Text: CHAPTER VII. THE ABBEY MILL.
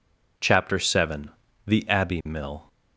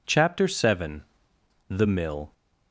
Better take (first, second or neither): first